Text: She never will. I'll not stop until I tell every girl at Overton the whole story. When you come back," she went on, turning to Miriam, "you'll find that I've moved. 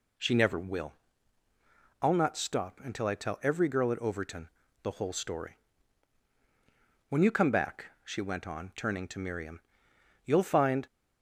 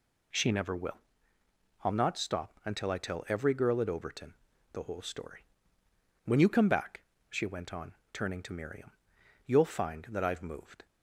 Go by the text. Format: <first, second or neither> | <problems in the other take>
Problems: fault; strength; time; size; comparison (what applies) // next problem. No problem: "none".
second | pauses between "Overton" and "the"; slight; at 4.4 s; 0.34 s long; also in the second // stops before "that I've moved"; at 10.8 s